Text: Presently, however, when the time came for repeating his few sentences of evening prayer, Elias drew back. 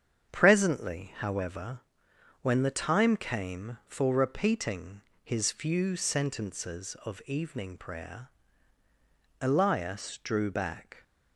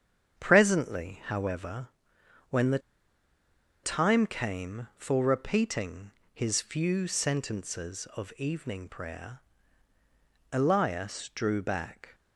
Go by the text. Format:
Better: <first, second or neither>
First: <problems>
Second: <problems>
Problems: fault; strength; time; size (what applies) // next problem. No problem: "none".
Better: first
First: starts louder than the rest; strong; until 1.3 s; 7.5 dB // pauses between "repeating" and "his"; slight; at 5.0 s; 0.22 s long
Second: starts louder than the rest; strong; until 1.4 s; 7.5 dB // pauses between "the" and "time"; at 2.7 s; 1.0 s long // pauses between "repeating" and "his"; slight; at 6.1 s; 0.22 s long